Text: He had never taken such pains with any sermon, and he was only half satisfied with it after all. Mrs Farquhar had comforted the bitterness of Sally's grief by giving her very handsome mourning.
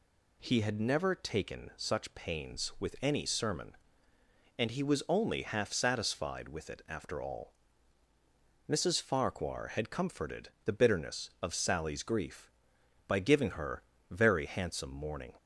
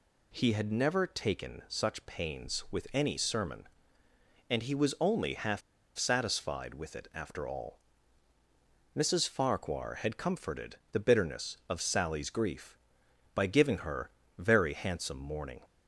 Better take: first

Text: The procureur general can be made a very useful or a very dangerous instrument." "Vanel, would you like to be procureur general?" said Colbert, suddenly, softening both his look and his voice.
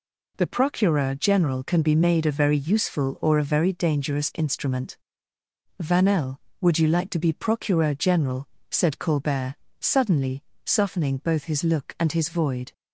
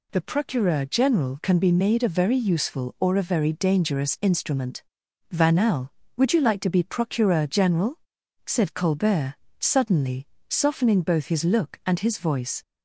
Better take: second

